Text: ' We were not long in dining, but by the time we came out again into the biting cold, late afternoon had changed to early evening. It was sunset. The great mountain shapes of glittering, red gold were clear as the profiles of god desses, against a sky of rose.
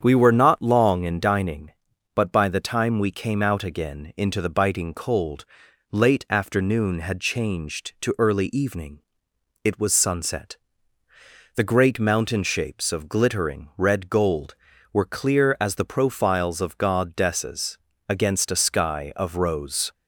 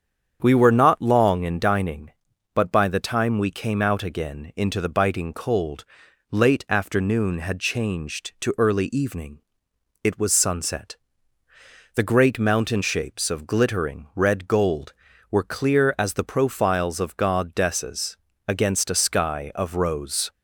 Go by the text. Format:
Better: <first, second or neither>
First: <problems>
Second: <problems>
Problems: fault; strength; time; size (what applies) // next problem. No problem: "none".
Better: neither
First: starts louder than the rest; strong; until 1.0 s; 8 dB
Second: starts louder than the rest; strong; until 1.4 s; 8 dB